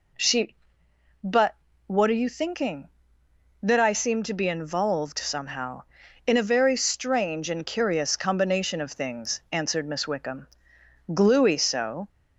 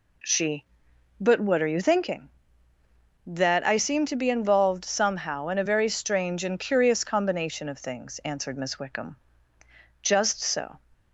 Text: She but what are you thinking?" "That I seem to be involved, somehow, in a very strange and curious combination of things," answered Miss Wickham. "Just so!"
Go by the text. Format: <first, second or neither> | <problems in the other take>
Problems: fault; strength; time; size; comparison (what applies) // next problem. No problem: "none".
second | pauses between "but" and "what"; slight; at 1.5 s; 0.32 s long // says "Gluey" for "Just"; at 11.1 s